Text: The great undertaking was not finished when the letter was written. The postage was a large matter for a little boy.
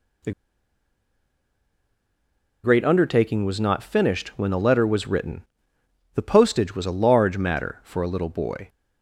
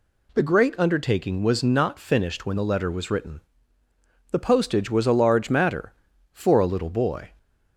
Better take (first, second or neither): second